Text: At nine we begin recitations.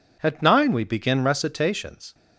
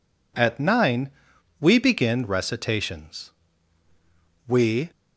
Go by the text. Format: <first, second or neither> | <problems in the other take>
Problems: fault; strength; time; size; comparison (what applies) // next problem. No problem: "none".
first | pauses between "nine" and "we"; noticeable; at 1.1 s; 0.50 s long // goes on to say "We"; slight; from 4.4 s on; 0.42 s long